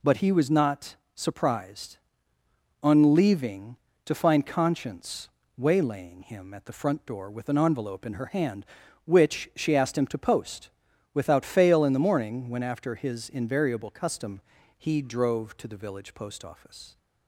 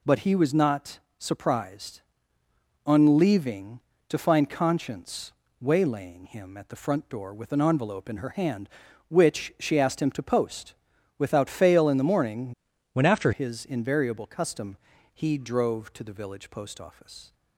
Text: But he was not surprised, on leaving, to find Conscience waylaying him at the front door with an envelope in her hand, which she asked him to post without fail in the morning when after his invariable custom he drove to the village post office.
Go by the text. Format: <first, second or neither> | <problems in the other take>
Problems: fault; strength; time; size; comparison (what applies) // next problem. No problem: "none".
first | pauses between "not" and "surprised"; slight; at 0.9 s; 0.18 s long; slight in the first // pauses between "Conscience" and "waylaying"; slight; at 5.3 s; 0.28 s long; slight in the first // pauses between "post" and "without"; at 10.7 s; 0.44 s long; also in the first // changes voice from "when" to "after"; from 12.9 to 13.3 s; 0.4 s long // pauses between "custom" and "he"; at 14.7 s; 0.38 s long; also in the first